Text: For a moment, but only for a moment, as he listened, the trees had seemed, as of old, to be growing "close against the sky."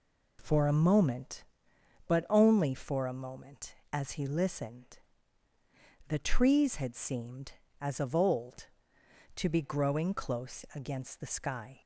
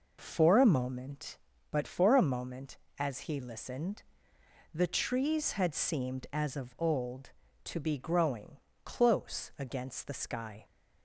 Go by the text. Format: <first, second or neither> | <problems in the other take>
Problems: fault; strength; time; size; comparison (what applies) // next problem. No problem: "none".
first | skips "only"; at 1.8 s // pauses between "growing" and "close"; slight; at 8.5 s; 0.26 s long